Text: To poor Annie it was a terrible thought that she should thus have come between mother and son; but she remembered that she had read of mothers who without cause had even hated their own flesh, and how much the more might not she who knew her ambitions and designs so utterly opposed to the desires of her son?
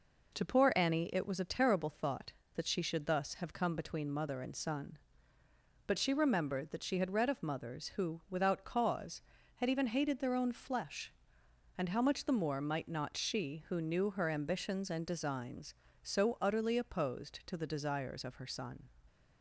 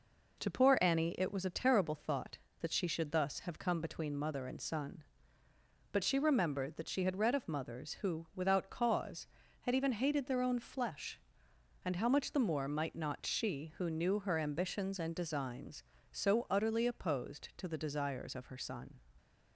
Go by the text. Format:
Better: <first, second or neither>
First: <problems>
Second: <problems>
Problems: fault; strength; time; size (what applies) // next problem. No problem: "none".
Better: neither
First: none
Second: none